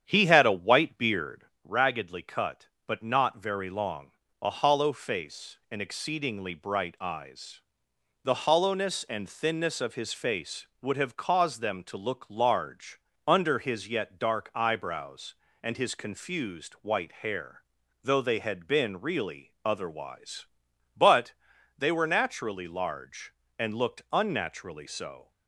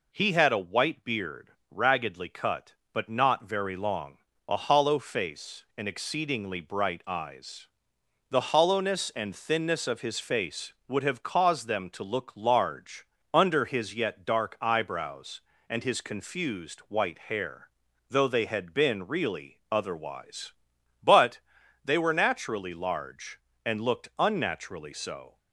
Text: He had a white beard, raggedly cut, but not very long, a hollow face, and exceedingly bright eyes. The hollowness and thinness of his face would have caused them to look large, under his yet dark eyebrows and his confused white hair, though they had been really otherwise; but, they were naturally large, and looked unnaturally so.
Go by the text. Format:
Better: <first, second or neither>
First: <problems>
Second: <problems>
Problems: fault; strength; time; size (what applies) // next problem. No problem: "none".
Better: second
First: starts louder than the rest; strong; until 1.5 s; 8.5 dB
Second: none